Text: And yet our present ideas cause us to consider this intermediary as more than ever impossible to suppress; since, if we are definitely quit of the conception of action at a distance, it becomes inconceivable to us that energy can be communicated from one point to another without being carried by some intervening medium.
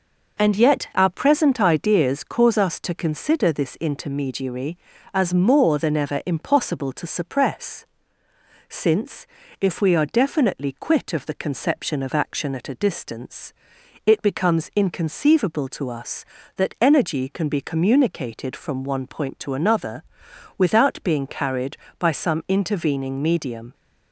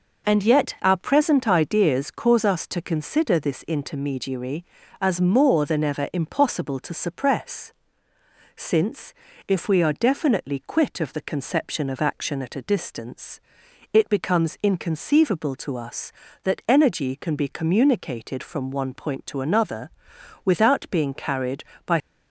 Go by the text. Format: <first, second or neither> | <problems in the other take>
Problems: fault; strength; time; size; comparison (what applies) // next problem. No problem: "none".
first | pauses between "another" and "without"; noticeable; at 19.8 s; 0.56 s long; noticeable in the first // stops before "some intervening medium"; at 22.0 s